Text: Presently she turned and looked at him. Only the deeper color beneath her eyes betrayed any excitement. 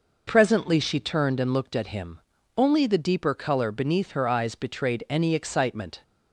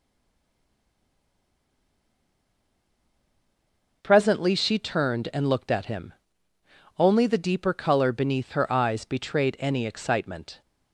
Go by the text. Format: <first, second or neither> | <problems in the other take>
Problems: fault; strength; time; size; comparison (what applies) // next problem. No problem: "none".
first | stays silent before the first word; strong; until 4.0 s; 4.0 s long